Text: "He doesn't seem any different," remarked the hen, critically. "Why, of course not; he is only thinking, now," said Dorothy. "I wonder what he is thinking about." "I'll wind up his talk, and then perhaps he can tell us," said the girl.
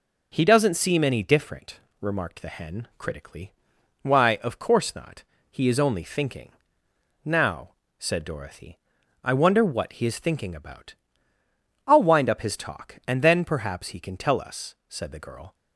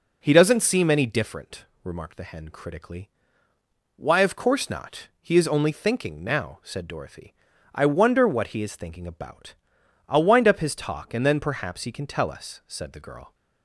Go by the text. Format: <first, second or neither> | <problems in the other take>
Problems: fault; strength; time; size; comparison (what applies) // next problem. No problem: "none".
neither | none